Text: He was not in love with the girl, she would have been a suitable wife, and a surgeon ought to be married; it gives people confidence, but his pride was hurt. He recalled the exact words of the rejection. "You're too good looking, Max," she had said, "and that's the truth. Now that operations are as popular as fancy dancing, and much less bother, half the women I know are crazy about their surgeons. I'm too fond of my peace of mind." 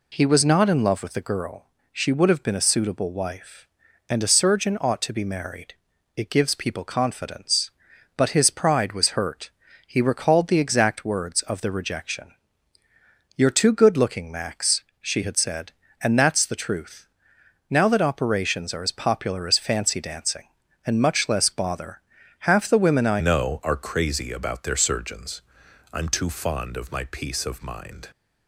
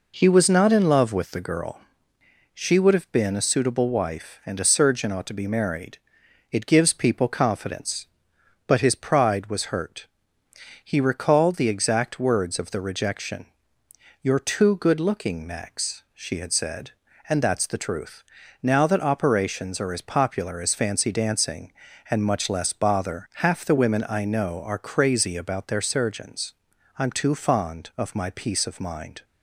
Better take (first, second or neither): second